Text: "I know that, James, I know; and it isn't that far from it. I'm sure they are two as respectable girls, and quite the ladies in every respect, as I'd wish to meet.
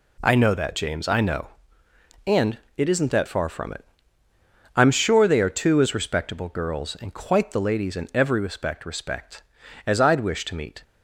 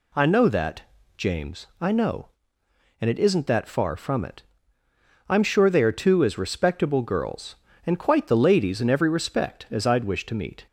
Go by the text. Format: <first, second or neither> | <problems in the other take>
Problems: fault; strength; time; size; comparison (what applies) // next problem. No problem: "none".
second | pauses between "and" and "it"; slight; at 2.5 s; 0.18 s long // says "respect" twice; at 8.8 s